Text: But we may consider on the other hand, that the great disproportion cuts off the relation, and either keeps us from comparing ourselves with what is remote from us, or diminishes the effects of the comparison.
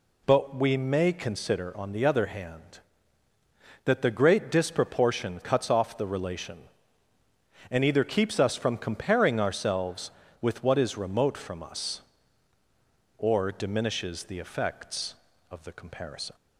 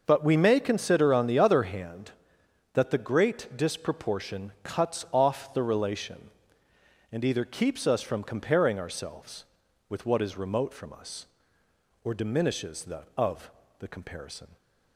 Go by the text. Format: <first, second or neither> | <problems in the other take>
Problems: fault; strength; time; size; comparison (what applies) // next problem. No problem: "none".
first | starts louder than the rest; noticeable; until 1.0 s; 6 dB // skips "effects"; at 13.1 s // pauses between "of" and "the"; slight; at 13.5 s; 0.28 s long